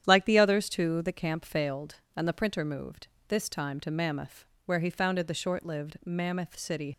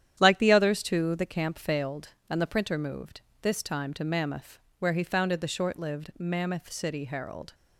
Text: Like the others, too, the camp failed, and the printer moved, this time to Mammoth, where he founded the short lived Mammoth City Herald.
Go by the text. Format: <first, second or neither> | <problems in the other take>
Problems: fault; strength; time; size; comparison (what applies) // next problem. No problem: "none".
second | starts louder than the rest; strong; until 1.0 s; 9.5 dB; strong in the second // stops before "Herald"; at 6.9 s